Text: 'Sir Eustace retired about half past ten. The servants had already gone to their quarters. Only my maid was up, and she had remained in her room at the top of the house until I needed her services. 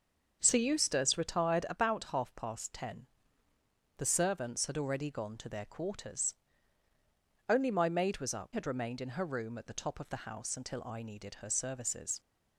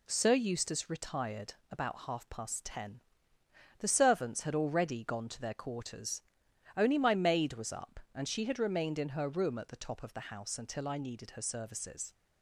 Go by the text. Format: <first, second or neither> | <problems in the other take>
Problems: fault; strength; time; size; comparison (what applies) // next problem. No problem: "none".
second | starts louder than the rest; until 1.4 s; 6.5 dB // skips "and she"; at 8.5 s